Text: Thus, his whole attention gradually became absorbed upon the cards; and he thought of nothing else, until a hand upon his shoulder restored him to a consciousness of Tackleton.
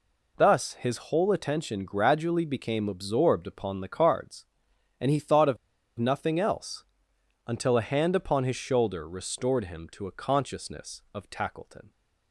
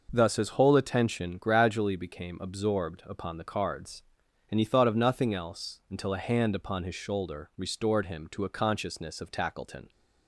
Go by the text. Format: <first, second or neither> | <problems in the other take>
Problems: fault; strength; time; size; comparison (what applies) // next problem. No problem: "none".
second | pauses between "of" and "nothing"; at 5.5 s; 0.42 s long